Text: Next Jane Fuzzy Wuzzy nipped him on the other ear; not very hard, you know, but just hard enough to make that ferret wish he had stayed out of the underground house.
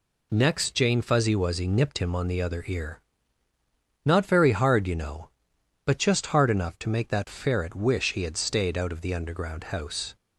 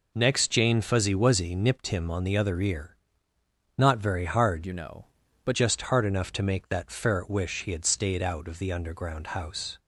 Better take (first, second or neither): first